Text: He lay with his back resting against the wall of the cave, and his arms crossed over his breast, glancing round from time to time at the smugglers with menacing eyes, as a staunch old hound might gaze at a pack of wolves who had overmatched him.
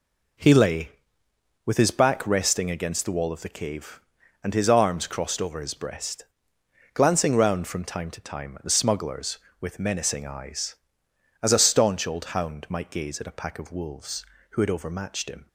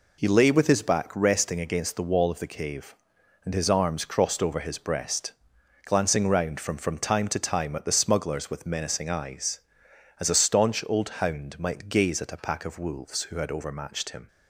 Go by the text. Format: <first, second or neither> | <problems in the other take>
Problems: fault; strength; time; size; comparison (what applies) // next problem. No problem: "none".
first | says "from" twice; at 6.7 s // pauses between "old" and "hound"; slight; at 11.0 s; 0.16 s long